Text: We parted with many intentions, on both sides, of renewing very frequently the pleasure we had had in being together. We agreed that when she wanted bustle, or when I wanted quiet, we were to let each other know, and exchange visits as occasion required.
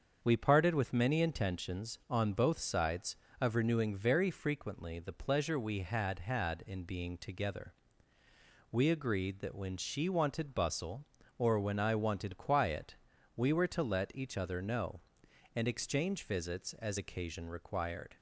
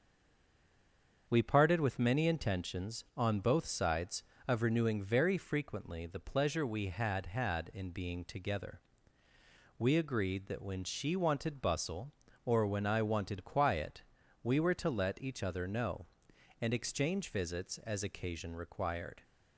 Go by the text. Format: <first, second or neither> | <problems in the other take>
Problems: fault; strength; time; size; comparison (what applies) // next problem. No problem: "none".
first | stays silent before the first word; noticeable; until 1.2 s; 1.2 s long // starts louder than the rest; until 2.2 s; 7 dB; also in the first